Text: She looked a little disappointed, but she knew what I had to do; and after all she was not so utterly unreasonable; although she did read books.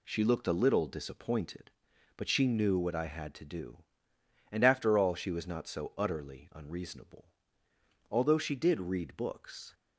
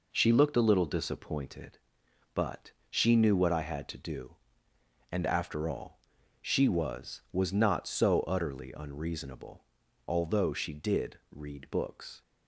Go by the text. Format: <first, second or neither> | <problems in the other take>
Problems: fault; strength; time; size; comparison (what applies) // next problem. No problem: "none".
first | pauses between "but" and "she"; slight; at 2.7 s; 0.18 s long // pauses between "all" and "she"; at 6.0 s; 0.42 s long // says "was" twice; at 7.3 s